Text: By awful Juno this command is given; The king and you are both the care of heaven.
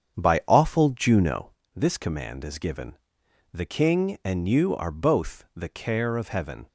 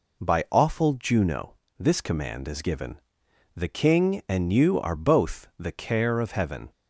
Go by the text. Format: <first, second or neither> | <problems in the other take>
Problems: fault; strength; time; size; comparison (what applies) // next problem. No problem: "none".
second | starts louder than the rest; strong; until 1.6 s; 8 dB // pauses between "Juno" and "this"; slight; at 1.5 s; 0.24 s long; slight in the second